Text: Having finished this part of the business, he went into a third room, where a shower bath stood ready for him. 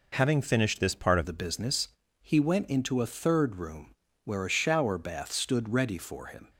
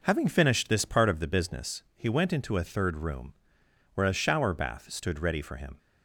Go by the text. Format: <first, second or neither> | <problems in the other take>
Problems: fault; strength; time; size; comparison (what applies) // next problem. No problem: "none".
second | changes voice at "the"; from 1.2 s on; 5.3 s long